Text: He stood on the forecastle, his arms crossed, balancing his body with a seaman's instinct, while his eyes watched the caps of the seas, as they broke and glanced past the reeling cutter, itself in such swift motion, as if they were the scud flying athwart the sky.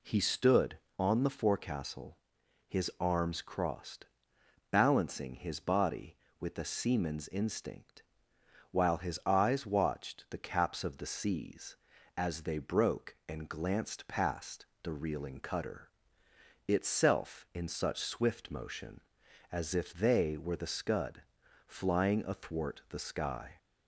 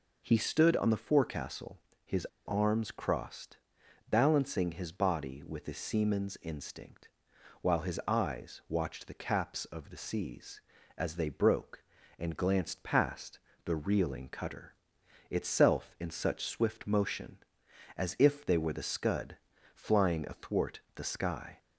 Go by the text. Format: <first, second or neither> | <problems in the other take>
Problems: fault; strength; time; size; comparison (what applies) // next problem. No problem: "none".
first | pauses between "his" and "arms"; slight; at 2.2 s; 0.21 s long // pauses between "past" and "the"; slight; at 13.4 s; 0.24 s long; slight in the first // pauses between "scud" and "flying"; slight; at 19.3 s; 0.36 s long; also in the first // pauses between "athwart" and "the"; slight; at 20.7 s; 0.16 s long